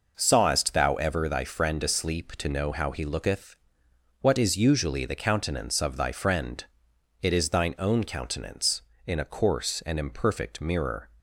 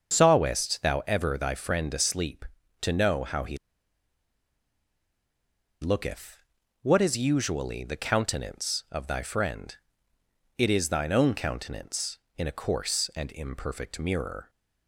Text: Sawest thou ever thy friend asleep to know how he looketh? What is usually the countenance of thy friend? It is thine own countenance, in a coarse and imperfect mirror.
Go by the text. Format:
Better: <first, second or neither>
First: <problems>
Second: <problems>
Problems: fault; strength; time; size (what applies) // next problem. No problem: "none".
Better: first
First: none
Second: starts louder than the rest; until 1.2 s; 6.5 dB // pauses between "he" and "looketh"; strong; at 3.5 s; 2.2 s long